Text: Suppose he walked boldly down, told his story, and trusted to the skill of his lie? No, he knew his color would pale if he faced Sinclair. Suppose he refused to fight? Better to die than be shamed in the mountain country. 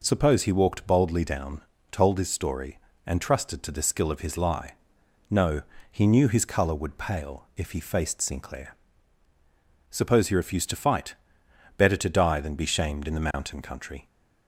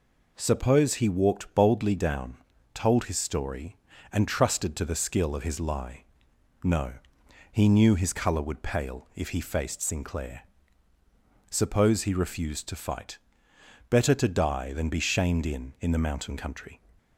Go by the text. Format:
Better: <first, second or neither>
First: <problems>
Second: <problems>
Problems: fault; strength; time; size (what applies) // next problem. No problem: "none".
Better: first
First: none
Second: says "in" twice; at 15.7 s